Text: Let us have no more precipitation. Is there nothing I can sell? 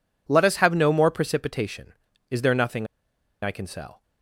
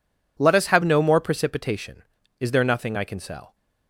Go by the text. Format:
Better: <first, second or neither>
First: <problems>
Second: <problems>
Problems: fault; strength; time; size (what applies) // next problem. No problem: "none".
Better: second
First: pauses between "nothing" and "I"; noticeable; at 2.8 s; 0.57 s long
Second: none